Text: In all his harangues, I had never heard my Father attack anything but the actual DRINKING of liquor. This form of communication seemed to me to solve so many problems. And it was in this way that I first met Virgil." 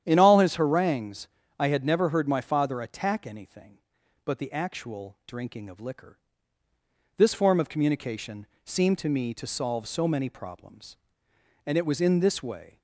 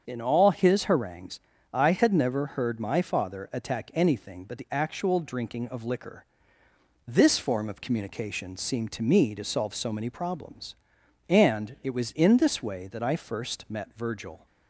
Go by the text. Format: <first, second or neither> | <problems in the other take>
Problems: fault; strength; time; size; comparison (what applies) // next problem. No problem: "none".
second | starts louder than the rest; strong; until 1.0 s; 10 dB; also in the second // pauses between "communication" and "seemed"; slight; at 8.4 s; 0.18 s long // stops before "that I first met Virgil"; at 12.7 s